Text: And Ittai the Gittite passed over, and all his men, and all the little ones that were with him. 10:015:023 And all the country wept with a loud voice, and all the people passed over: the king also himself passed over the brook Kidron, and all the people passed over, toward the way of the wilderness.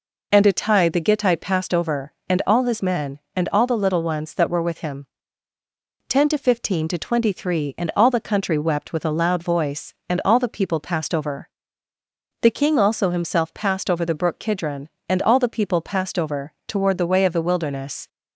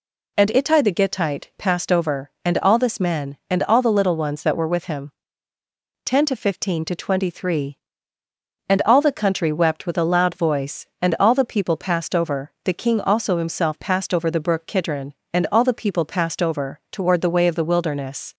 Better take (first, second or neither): first